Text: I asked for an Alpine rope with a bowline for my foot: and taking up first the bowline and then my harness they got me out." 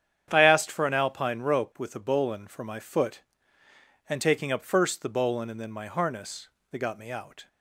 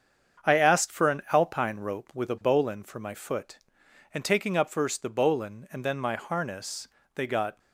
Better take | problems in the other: first | starts louder than the rest; strong; until 1.5 s; 7.5 dB; strong in the first // pauses between "harness" and "they"; slight; at 6.8 s; 0.26 s long; slight in the first // stops before "me out"; at 7.5 s

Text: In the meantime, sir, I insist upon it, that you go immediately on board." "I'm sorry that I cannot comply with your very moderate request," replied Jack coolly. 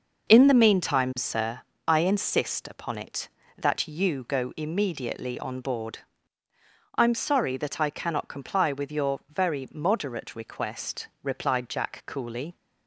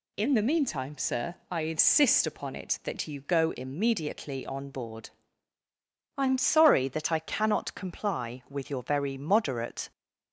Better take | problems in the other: first | stops before "request replied Jack coolly"; at 9.9 s

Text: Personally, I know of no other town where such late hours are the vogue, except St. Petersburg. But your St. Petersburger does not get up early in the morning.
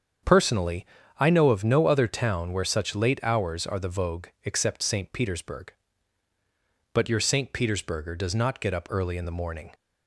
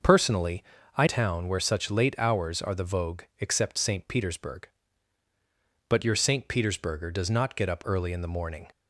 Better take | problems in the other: first | starts louder than the rest; until 1.3 s; 6 dB; strong in the first // skips "know of no other"; at 1.0 s

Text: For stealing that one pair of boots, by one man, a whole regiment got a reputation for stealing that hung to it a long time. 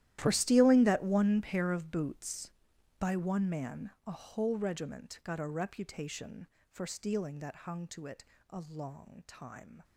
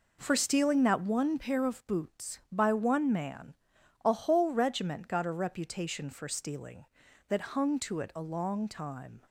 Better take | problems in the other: second | gets quieter; strong; throughout; 19 dB // pauses between "it" and "a"; slight; at 8.2 s; 0.24 s long

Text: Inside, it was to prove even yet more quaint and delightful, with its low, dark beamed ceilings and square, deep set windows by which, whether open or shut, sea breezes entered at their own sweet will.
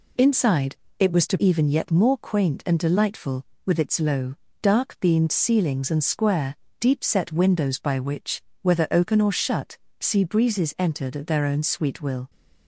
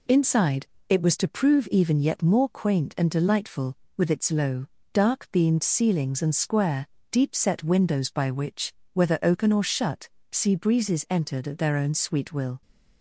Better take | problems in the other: second | skips "prove"; at 1.3 s

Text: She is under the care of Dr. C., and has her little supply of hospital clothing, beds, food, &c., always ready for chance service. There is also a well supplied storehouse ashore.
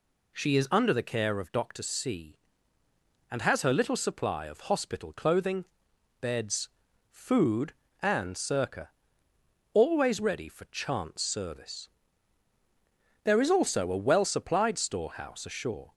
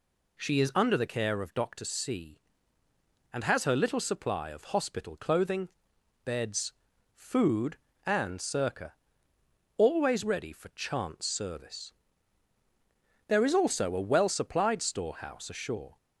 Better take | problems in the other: neither | none

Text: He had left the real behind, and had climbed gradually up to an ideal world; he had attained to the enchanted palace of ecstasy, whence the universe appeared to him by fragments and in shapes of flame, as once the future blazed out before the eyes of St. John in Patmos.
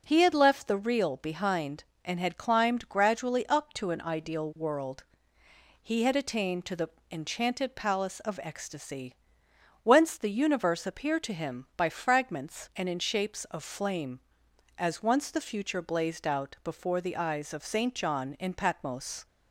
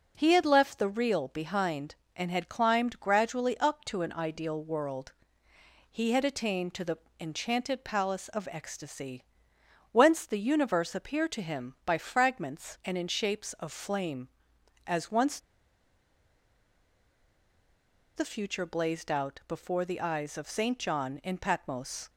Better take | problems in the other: first | pauses between "the" and "enchanted"; slight; at 6.9 s; 0.24 s long; slight in the first // pauses between "once" and "the"; strong; at 15.3 s; 2.7 s long

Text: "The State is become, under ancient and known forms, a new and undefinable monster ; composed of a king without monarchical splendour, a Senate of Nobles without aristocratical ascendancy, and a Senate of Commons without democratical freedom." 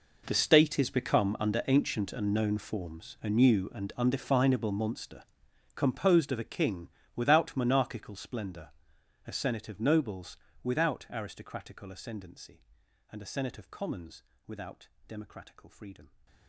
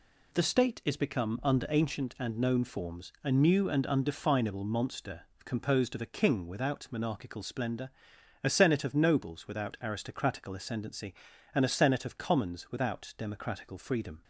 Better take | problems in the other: second | gets quieter; strong; throughout; 18 dB // pauses between "king" and "without"; slight; at 6.8 s; 0.26 s long // pauses between "Nobles" and "without"; slight; at 10.3 s; 0.26 s long // pauses between "Commons" and "without"; slight; at 14.2 s; 0.24 s long // pauses between "without" and "democratical"; slight; at 14.8 s; 0.20 s long

